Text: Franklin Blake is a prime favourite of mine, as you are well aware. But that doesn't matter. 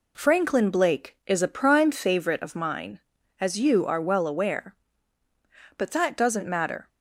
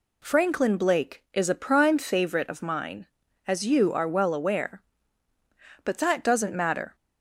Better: second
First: gets quieter; noticeable; throughout; 4 dB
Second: none

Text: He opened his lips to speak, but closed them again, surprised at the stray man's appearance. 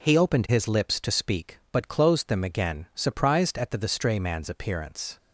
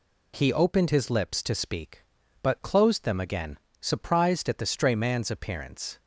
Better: second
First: says "the" twice; at 3.7 s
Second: none

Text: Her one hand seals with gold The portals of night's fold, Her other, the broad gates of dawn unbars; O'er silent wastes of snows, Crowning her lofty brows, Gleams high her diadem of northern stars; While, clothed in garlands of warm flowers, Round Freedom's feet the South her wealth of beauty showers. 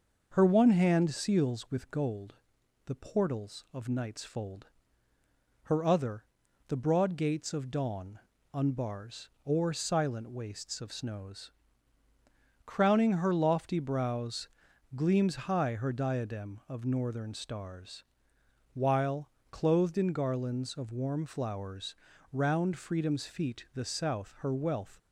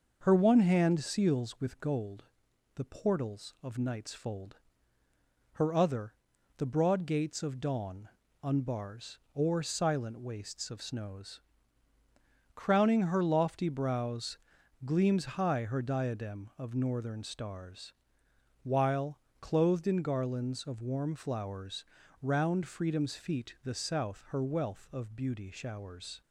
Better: second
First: pauses between "gold" and "The"; noticeable; at 2.3 s; 0.54 s long // pauses between "dawn" and "unbars"; slight; at 8.1 s; 0.36 s long // stops before "of beauty showers"; at 24.9 s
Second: pauses between "gold" and "The"; noticeable; at 2.2 s; 0.54 s long // pauses between "dawn" and "unbars"; slight; at 8.0 s; 0.36 s long

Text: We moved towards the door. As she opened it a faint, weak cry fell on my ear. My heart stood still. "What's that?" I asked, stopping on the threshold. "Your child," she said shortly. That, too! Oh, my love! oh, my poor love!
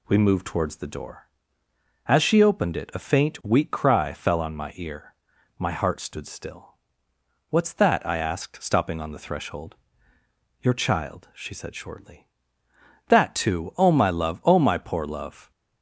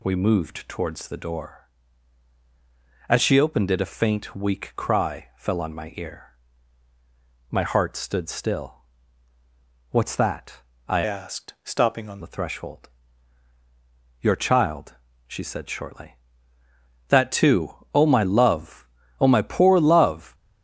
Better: first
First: none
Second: changes voice from "asked" to "on"; from 11.0 to 12.2 s; 1.2 s long

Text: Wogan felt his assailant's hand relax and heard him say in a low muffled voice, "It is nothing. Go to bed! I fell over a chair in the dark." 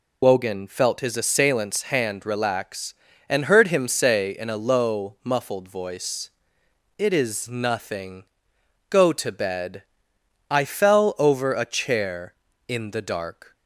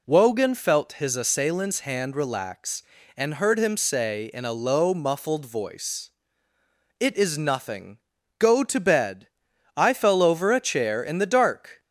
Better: second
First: loses the start of "Wogan"; at 0.2 s; 45 ms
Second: none

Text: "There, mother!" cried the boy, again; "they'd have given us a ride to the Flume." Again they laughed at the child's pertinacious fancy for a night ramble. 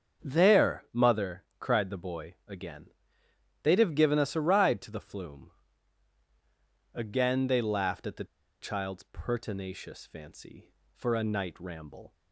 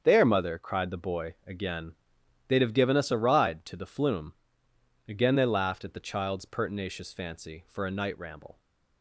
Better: second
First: starts louder than the rest; until 1.3 s; 7 dB // pauses between "the" and "child's"; at 8.2 s; 0.37 s long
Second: starts louder than the rest; until 1.0 s; 7 dB

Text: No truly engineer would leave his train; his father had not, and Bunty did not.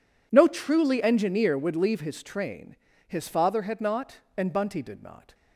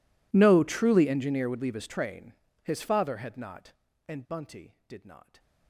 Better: first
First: none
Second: gets quieter; strong; throughout; 30 dB

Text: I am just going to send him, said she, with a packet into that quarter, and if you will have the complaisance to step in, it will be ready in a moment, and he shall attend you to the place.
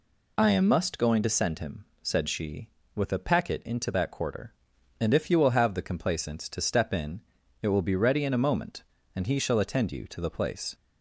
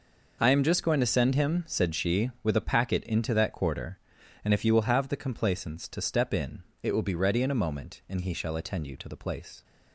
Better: second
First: says "must" for "just"; at 0.6 s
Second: none

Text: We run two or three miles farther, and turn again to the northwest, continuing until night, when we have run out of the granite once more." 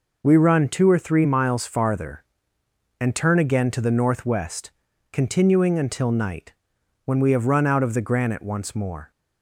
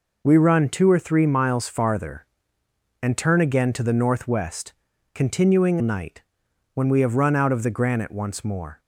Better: first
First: none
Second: skips "until"; at 5.8 s

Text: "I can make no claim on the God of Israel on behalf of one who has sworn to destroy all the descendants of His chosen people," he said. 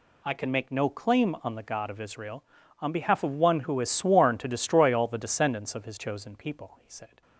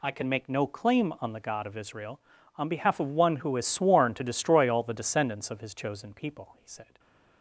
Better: neither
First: none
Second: none

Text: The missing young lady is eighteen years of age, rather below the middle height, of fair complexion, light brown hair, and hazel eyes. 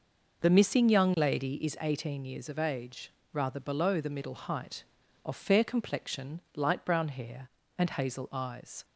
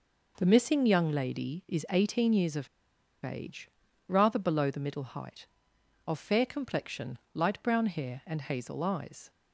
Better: first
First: none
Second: pauses between "of" and "age"; noticeable; at 2.6 s; 0.56 s long

